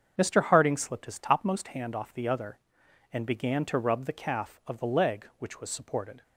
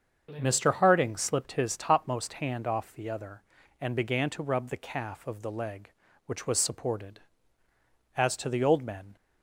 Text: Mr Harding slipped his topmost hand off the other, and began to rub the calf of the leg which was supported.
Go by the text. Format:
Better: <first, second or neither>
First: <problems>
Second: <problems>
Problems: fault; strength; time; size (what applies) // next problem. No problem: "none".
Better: first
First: starts louder than the rest; until 1.1 s; 7 dB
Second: starts louder than the rest; until 1.4 s; 7 dB // goes on to say "As to the old men"; noticeable; from 8.1 s on; 1.0 s long